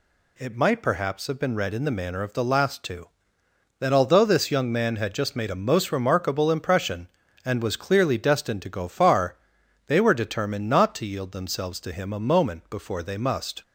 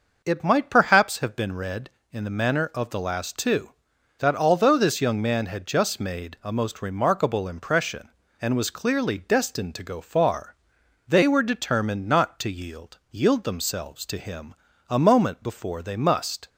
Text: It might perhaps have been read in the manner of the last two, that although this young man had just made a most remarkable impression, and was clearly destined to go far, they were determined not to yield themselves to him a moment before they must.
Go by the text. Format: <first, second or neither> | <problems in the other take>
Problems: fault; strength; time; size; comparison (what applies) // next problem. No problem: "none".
first | says "yield" twice; at 13.1 s // pauses between "him" and "a"; slight; at 14.5 s; 0.34 s long